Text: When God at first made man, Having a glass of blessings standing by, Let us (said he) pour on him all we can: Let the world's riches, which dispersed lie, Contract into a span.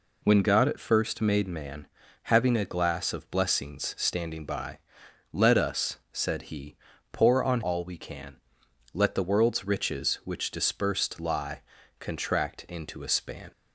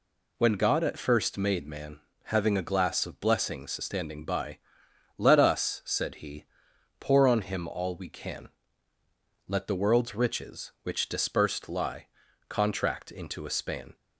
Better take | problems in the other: second | skips "him"; at 7.6 s

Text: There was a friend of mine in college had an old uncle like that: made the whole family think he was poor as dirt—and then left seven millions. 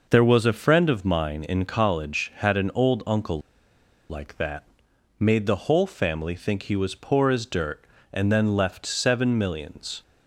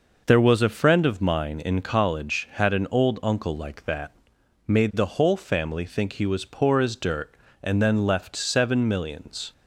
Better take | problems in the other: second | pauses between "uncle" and "like"; noticeable; at 3.4 s; 0.68 s long

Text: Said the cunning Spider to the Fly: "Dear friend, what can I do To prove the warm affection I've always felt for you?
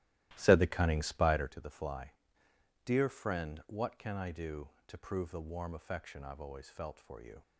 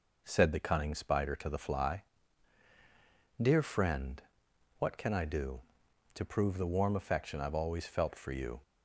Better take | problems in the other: second | starts louder than the rest; strong; until 1.7 s; 15 dB

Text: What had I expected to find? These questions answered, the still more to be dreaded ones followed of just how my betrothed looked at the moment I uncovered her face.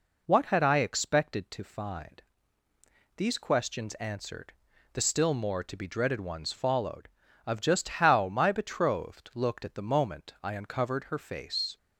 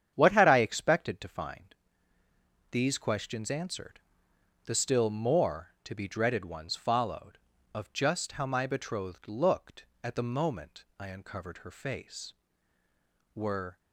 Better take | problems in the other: first | starts louder than the rest; strong; until 1.1 s; 8.5 dB // goes on to say "Were"; slight; from 13.3 s on; 0.44 s long

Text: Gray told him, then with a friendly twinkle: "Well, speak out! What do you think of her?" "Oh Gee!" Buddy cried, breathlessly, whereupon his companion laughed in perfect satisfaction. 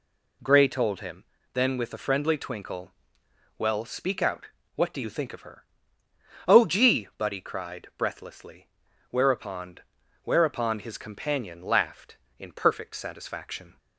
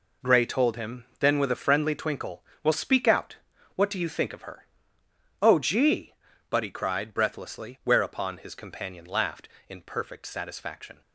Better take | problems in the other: second | says "whereupon" twice; at 10.2 s

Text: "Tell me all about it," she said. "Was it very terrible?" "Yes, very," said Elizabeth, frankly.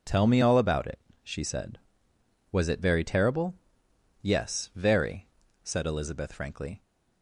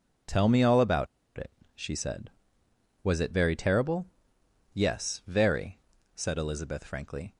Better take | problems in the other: first | pauses between "about" and "it"; slight; at 1.0 s; 0.30 s long

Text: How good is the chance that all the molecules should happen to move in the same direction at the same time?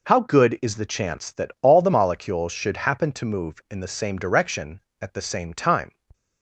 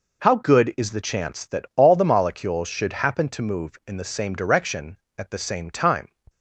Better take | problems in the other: neither | none

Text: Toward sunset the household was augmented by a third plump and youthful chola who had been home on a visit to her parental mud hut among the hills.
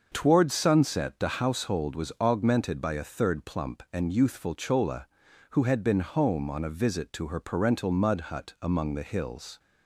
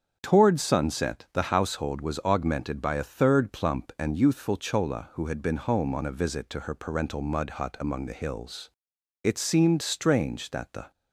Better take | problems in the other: first | starts louder than the rest; strong; until 1.2 s; 7.5 dB; also in the first // goes on to say "It seemed strange that the"; strong; from 9.2 s on; 1.6 s long

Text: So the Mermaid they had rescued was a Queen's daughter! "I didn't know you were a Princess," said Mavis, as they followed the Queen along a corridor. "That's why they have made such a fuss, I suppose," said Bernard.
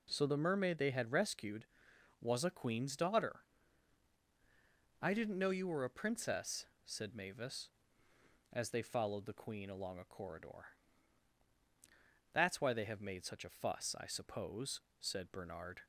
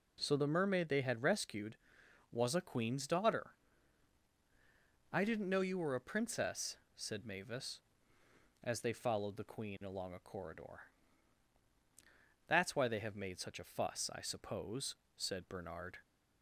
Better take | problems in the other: neither | none

